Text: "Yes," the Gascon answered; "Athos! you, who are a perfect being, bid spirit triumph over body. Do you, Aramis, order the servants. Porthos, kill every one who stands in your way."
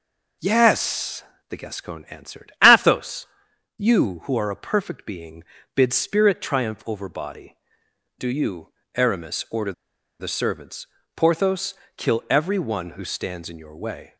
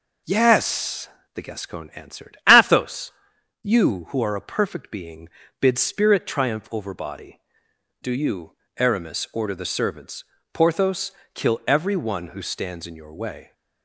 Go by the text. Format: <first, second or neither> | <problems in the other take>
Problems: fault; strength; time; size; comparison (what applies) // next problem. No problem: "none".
second | pauses between "order" and "the"; noticeable; at 9.7 s; 0.47 s long